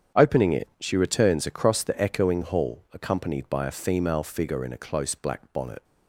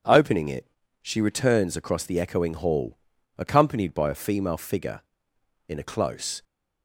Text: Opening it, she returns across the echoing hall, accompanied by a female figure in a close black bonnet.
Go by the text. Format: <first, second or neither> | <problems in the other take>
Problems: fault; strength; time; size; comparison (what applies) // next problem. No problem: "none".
first | starts louder than the rest; strong; until 1.3 s; 7.5 dB; strong in the first // stops before "black bonnet"; at 6.4 s